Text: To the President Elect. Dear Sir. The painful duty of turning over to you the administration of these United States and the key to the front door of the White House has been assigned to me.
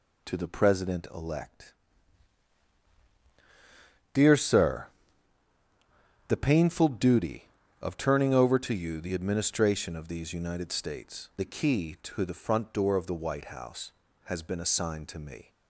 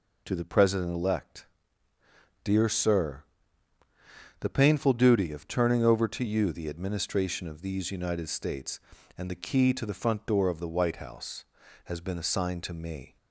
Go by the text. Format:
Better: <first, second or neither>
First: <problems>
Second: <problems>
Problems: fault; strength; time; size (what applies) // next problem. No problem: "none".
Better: second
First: skips "and"; at 11.3 s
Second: none